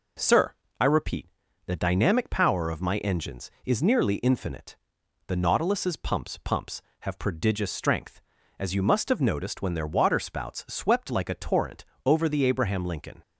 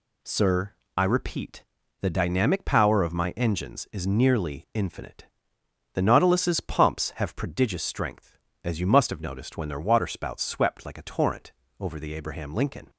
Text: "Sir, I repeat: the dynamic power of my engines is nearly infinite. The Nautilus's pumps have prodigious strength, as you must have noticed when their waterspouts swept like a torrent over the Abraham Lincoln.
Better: second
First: says "pumps" twice; at 6.4 s // pauses between "torrent" and "over"; slight; at 11.8 s; 0.22 s long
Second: pauses between "torrent" and "over"; slight; at 11.5 s; 0.26 s long

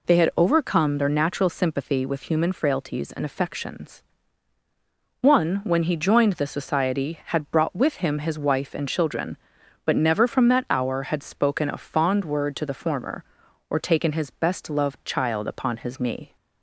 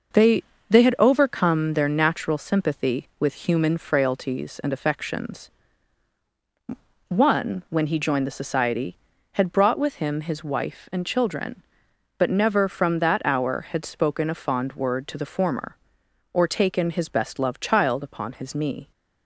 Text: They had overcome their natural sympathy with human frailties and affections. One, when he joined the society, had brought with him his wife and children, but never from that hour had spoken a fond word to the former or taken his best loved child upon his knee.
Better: first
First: none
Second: says "They" twice; at 0.6 s

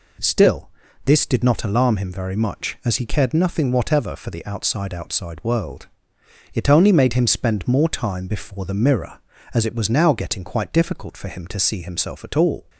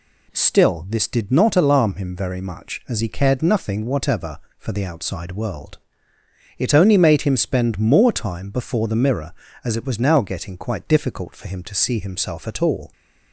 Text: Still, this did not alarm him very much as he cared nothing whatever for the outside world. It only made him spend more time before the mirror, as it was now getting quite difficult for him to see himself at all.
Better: second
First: says "outside" twice; at 4.9 s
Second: none

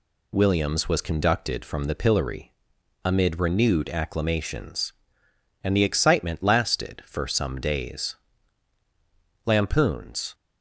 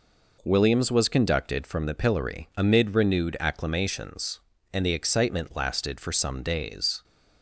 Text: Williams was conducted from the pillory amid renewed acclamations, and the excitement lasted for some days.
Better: second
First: pauses between "pillory" and "amid"; noticeable; at 2.4 s; 0.54 s long // goes on to say "Lampoons"; noticeable; from 9.4 s on; 0.88 s long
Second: none

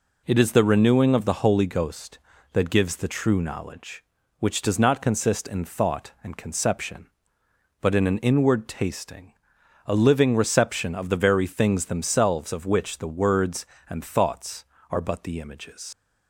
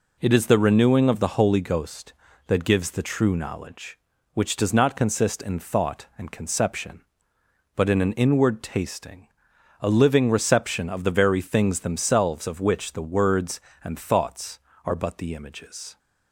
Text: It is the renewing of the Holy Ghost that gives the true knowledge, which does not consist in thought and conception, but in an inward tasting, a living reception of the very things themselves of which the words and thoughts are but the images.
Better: second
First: leaves "images" unfinished; at 15.9 s; 105 ms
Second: none

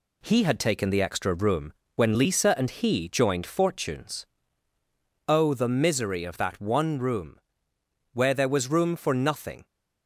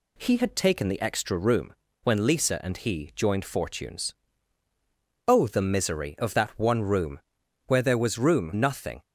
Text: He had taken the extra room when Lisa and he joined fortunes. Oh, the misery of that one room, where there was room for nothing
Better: first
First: pauses between "room" and "when"; slight; at 1.7 s; 0.24 s long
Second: pauses between "room" and "when"; slight; at 1.7 s; 0.30 s long // skips "for"; at 8.5 s

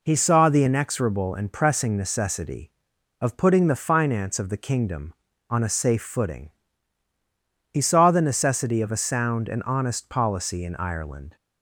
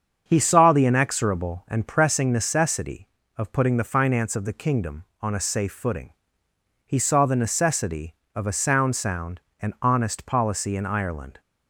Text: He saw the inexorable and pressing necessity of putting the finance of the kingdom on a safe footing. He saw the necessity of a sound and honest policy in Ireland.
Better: first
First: none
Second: starts louder than the rest; until 1.2 s; 7 dB // says "sound" twice; at 8.9 s

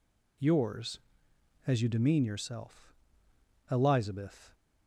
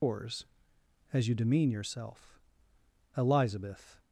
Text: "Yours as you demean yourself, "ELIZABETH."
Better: first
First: none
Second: loses the start of "Yours"; at 0.0 s; 165 ms

